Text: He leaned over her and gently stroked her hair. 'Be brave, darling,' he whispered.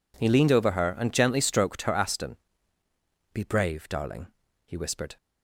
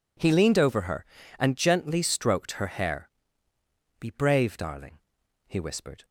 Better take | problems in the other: second | says "aston" for "hair"; at 1.9 s

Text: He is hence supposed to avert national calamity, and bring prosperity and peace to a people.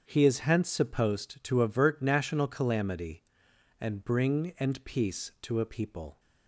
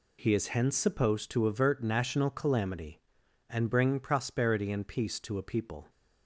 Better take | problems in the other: second | starts louder than the rest; strong; until 1.0 s; 7.5 dB // skips "prosperity"; at 4.5 s

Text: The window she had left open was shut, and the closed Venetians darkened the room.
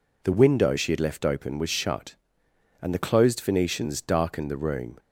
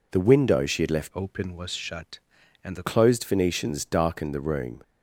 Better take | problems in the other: first | changes voice from "open" to "the"; from 1.1 to 2.8 s; 1.7 s long

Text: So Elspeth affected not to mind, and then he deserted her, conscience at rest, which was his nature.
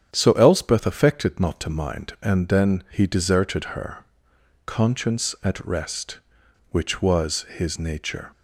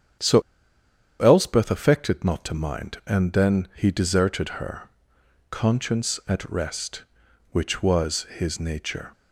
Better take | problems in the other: first | starts louder than the rest; strong; until 2.0 s; 8.5 dB; strong in the first // pauses between "So" and "Elspeth"; noticeable; at 0.4 s; 0.79 s long

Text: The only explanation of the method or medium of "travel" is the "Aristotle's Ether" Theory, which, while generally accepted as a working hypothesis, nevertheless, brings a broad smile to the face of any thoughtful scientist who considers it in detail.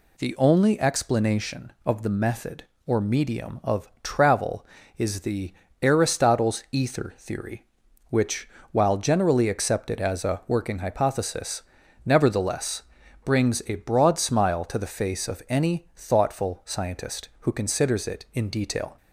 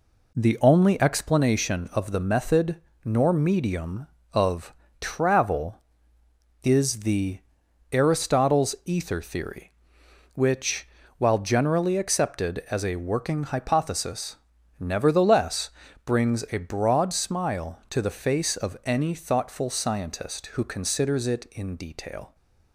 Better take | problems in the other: first | says "nor" for "or"; at 3.0 s // pauses between "of" and "travel"; slight; at 4.7 s; 0.26 s long; slight in the first // pauses between "the" and "Aristotle's"; noticeable; at 7.3 s; 0.52 s long; slight in the first

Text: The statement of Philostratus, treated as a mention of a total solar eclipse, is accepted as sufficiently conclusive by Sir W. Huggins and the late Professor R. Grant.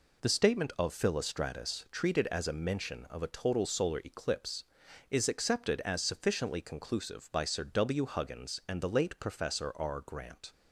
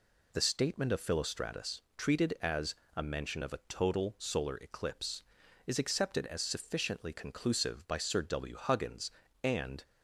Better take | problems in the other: first | pauses between "as" and "a"; slight; at 2.7 s; 0.20 s long // stops before "the late Professor R Grant"; at 9.8 s

